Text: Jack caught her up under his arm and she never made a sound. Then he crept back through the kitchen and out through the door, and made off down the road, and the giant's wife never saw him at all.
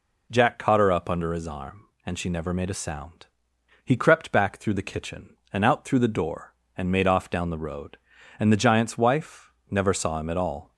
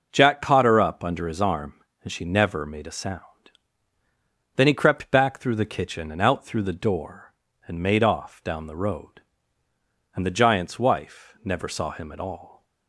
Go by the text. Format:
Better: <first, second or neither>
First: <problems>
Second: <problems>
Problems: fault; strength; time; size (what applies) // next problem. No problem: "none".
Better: second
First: skips "Then"; at 3.5 s // pauses between "wife" and "never"; slight; at 9.5 s; 0.18 s long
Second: none